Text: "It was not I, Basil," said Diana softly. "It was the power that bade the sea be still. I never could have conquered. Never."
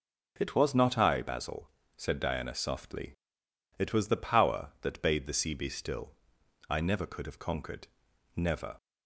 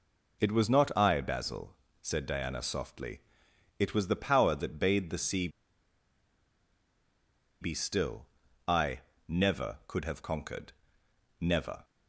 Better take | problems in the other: first | pauses between "sea" and "be"; strong; at 5.4 s; 2.1 s long // pauses between "I" and "never"; slight; at 9.0 s; 0.28 s long

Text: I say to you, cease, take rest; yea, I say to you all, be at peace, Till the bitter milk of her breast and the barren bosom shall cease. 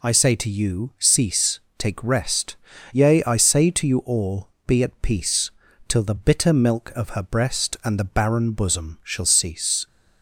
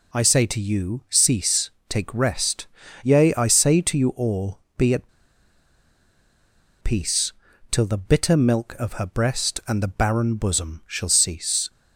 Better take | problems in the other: first | pauses between "at" and "peace"; strong; at 5.0 s; 1.7 s long

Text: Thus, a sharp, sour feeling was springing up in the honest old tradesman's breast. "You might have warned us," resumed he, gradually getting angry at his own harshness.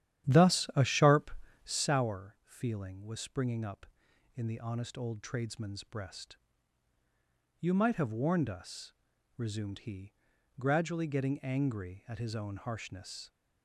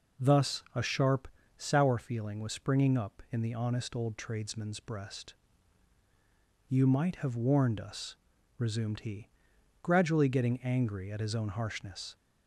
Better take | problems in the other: second | starts louder than the rest; strong; until 1.9 s; 11 dB

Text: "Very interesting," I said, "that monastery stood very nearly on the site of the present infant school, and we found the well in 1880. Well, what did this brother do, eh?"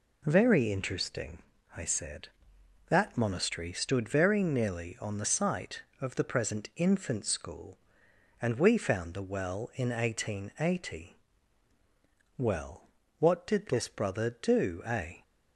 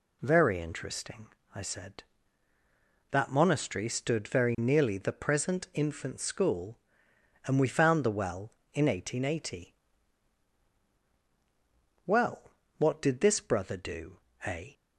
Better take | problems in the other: first | skips "on the site of"; at 4.9 s

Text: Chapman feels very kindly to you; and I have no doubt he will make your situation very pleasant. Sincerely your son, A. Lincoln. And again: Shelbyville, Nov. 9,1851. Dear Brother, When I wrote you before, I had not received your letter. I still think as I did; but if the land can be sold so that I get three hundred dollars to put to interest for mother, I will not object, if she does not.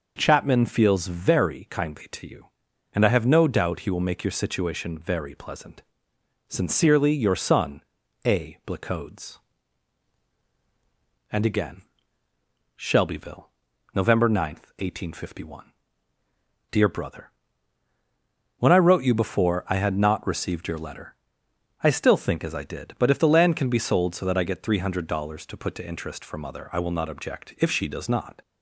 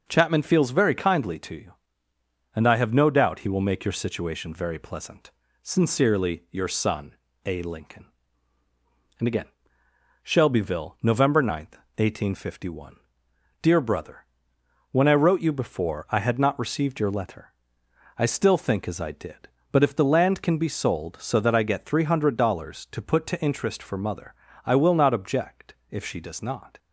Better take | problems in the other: second | says "Blacodes" for "Lincoln"; at 8.6 s

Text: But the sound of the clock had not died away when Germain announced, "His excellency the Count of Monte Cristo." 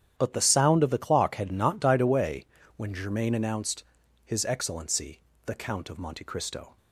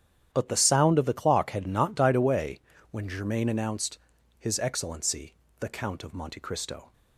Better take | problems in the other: neither | starts louder than the rest; strong; the same in both // pauses between "away" and "when"; slight; the same in both // pauses between "excellency" and "the"; slight; the same in both

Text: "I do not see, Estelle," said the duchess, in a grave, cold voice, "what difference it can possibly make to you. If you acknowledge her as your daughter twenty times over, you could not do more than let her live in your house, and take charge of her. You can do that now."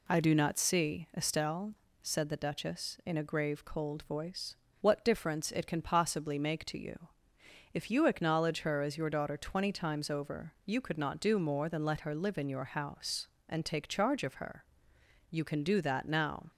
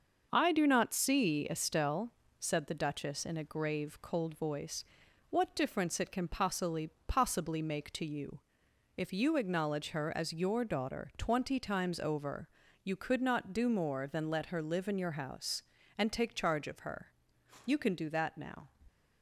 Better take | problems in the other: first | starts louder than the rest; until 1.3 s; 6 dB // says "possibly" twice; at 7.0 s

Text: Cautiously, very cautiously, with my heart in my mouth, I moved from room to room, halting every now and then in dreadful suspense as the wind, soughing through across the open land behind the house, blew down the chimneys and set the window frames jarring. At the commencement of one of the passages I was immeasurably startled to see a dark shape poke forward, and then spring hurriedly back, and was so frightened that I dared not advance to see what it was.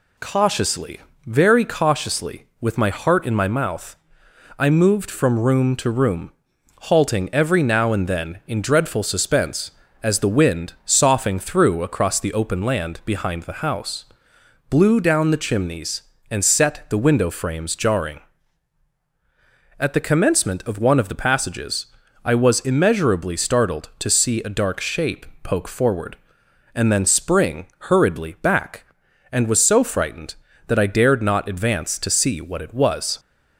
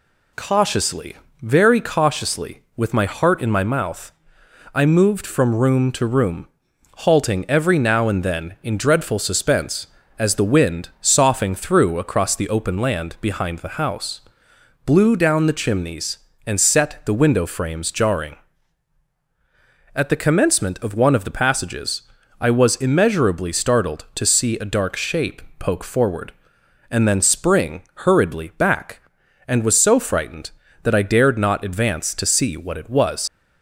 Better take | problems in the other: first | pauses between "passages" and "I"; at 22.0 s; 0.38 s long; also in the first // pauses between "shape" and "poke"; slight; at 25.4 s; 0.16 s long; slight in the first // leaves "was" unfinished; at 33.2 s; 75 ms

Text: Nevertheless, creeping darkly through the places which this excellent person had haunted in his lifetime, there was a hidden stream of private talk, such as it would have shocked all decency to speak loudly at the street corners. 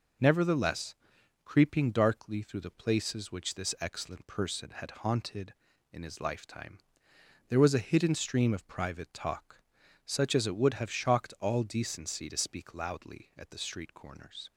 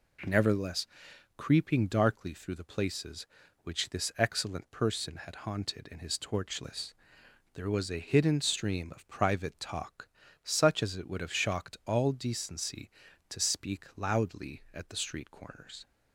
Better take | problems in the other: first | says "torchless" for "lifetime"; at 6.1 s

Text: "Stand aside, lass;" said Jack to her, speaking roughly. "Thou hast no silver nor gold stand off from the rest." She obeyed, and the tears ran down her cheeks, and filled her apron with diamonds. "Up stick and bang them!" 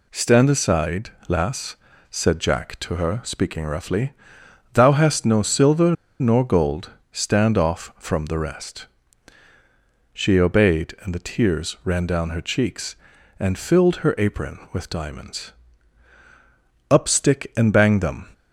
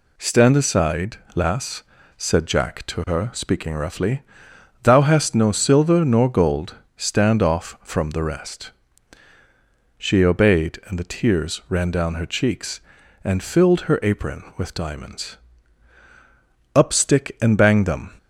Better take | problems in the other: second | pauses between "silver" and "nor"; slight; at 5.9 s; 0.25 s long // pauses between "gold" and "stand"; slight; at 6.8 s; 0.22 s long; slight in the second

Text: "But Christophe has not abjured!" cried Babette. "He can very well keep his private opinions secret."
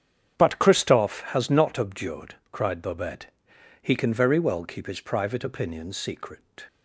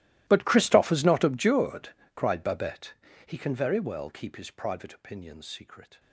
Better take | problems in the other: first | gets quieter; strong; throughout; 23 dB // starts louder than the rest; strong; until 1.2 s; 16 dB; strong in the first

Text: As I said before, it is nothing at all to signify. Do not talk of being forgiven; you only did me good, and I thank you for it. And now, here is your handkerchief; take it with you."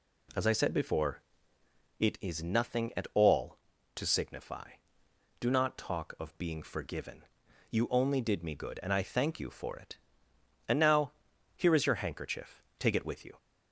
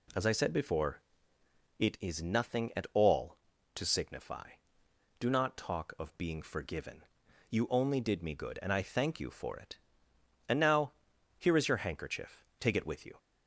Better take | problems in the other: neither | none

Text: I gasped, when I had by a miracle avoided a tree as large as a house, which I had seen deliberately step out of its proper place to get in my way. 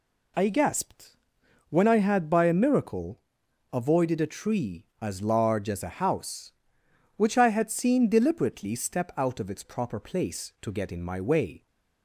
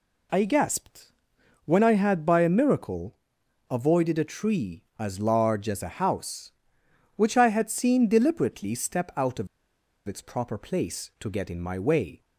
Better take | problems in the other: first | pauses between "miracle" and "avoided"; noticeable; at 3.1 s; 0.54 s long; noticeable in the first // pauses between "of" and "its"; noticeable; at 9.4 s; 0.61 s long

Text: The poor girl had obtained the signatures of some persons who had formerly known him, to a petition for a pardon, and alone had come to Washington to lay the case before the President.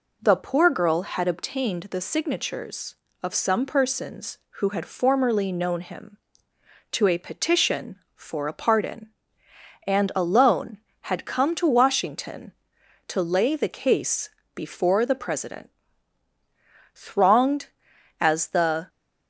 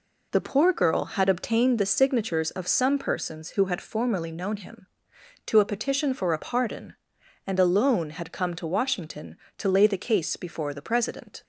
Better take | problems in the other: second | pauses between "case" and "before"; slight; at 14.2 s; 0.26 s long // goes on to say "Thronged as the"; strong; from 16.9 s on; 1.9 s long

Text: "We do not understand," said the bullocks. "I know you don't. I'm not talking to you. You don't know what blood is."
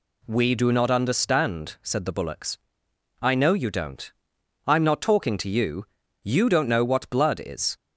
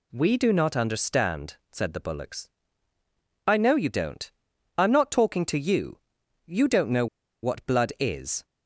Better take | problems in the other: first | pauses between "know" and "what"; at 7.0 s; 0.36 s long

